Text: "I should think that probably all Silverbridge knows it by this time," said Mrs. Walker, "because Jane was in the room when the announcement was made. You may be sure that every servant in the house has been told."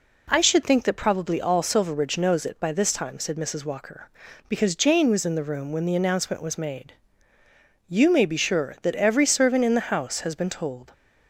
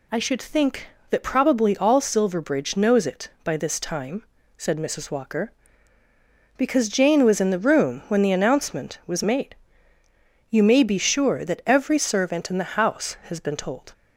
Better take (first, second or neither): neither